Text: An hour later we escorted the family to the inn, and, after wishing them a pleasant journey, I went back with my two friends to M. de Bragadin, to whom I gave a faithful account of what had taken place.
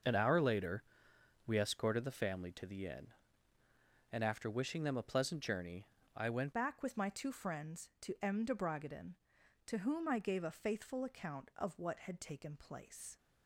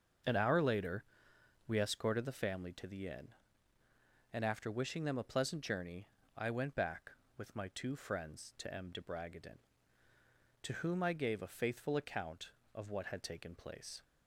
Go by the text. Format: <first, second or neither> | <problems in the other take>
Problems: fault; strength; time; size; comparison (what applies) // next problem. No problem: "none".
second | starts louder than the rest; until 1.6 s; 6 dB; also in the second // pauses between "later" and "we"; noticeable; at 0.8 s; 0.62 s long; noticeable in the second // changes voice at "back"; from 6.5 s on; 6.6 s long